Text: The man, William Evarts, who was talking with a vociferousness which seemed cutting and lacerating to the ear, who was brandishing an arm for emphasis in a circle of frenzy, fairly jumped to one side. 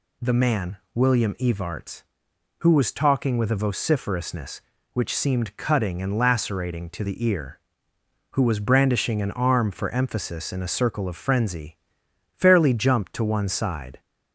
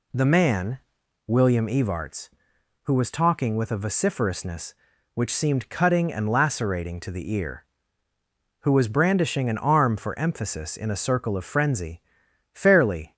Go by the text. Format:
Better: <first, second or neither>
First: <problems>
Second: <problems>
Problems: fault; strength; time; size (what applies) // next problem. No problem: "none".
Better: first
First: none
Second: stops before "jumped to one side"; at 13.1 s